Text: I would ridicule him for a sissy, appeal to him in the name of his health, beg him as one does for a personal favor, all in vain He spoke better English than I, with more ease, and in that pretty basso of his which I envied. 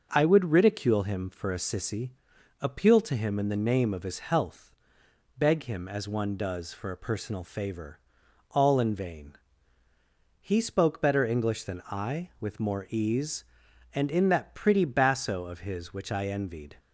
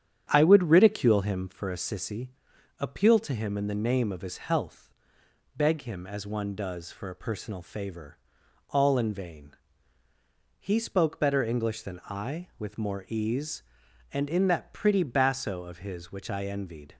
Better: first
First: pauses between "vain" and "He"; at 9.3 s; 1.0 s long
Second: starts louder than the rest; strong; until 1.7 s; 9 dB // pauses between "vain" and "He"; at 9.5 s; 1.0 s long

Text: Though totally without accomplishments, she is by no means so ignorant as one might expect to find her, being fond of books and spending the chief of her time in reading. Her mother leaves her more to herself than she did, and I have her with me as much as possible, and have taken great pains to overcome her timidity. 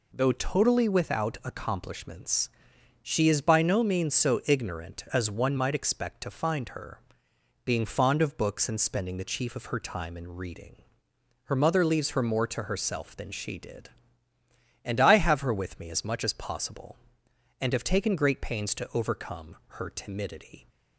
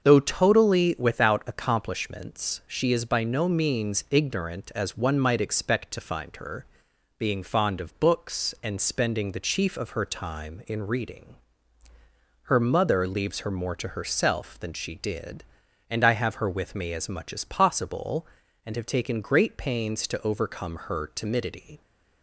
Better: first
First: none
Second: starts louder than the rest; until 1.0 s; 7 dB // skips "so"; at 4.0 s

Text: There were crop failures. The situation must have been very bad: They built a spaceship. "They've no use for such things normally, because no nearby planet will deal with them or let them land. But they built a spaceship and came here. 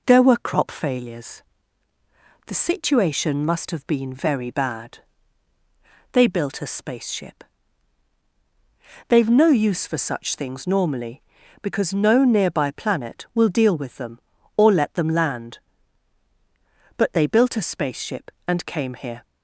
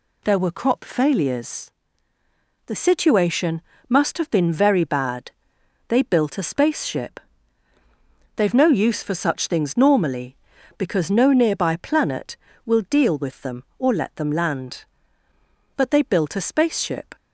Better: first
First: none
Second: pauses between "situation" and "must"; slight; at 3.6 s; 0.26 s long // stops before "and came here"; at 17.1 s

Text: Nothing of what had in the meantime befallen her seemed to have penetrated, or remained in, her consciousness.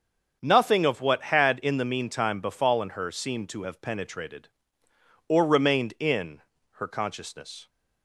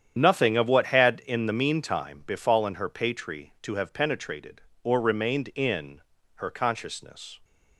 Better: first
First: starts louder than the rest; until 1.4 s; 7 dB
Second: starts louder than the rest; strong; until 1.2 s; 9 dB // says "patri" for "seemed"; at 2.8 s

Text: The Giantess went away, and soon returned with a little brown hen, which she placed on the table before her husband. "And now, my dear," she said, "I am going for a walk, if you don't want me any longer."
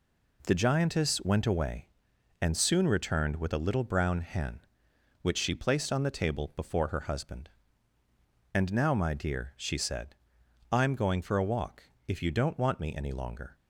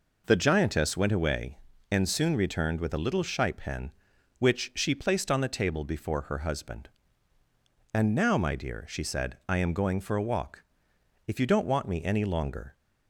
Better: first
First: none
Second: says "shipe" for "brown"; at 3.2 s

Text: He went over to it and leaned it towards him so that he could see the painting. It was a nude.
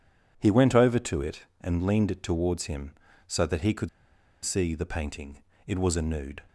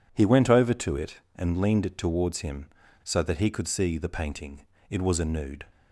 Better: second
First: pauses between "could" and "see"; noticeable; at 3.8 s; 0.56 s long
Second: none

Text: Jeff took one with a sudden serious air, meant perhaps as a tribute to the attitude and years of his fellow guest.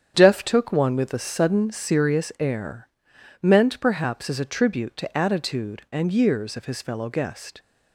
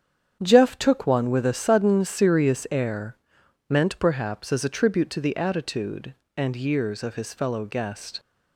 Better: second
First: starts louder than the rest; strong; until 1.1 s; 8.5 dB // skips "the"; at 5.1 s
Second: starts louder than the rest; strong; until 1.4 s; 8.5 dB

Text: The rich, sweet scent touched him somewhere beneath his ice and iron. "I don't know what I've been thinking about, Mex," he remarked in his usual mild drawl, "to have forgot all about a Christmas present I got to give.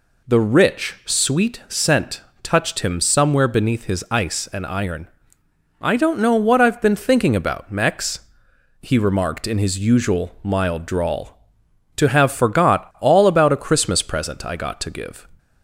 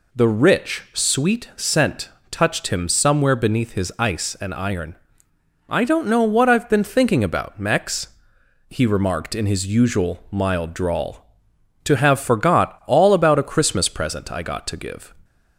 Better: neither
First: pauses between "scent" and "touched"; slight; at 2.2 s; 0.22 s long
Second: pauses between "scent" and "touched"; slight; at 2.0 s; 0.22 s long

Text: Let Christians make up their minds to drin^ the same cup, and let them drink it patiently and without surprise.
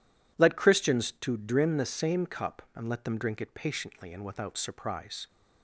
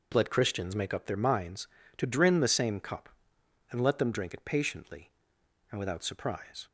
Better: second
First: skips "make up their minds"; at 1.1 s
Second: none

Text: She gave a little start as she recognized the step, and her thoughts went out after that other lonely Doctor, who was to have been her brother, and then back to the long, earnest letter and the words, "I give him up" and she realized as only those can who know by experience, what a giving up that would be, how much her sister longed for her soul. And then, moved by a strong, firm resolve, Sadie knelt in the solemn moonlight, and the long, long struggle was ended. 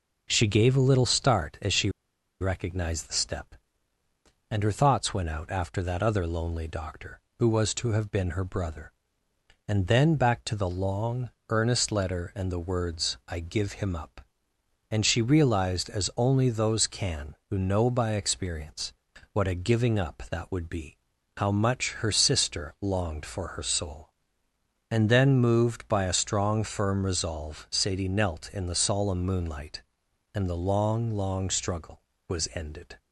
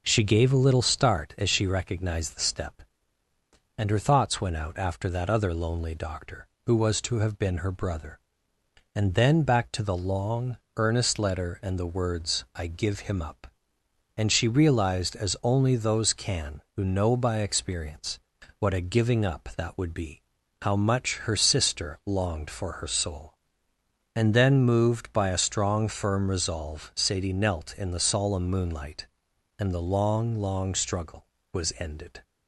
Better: second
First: pauses between "she" and "recognized"; noticeable; at 1.8 s; 0.51 s long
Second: none

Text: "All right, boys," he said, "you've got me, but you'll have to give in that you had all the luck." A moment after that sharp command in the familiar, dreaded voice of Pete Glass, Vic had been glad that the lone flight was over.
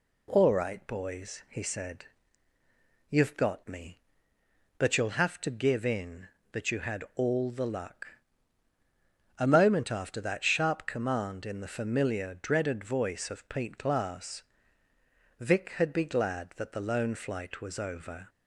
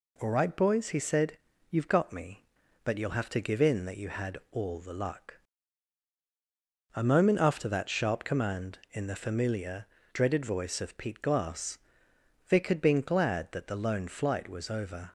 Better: second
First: says "be" for "been"; at 15.9 s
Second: none

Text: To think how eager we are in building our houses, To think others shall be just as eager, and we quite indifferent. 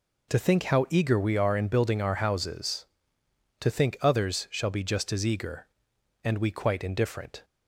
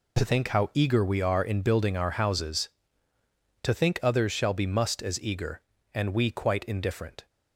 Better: first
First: none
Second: says "must" for "just"; at 4.6 s

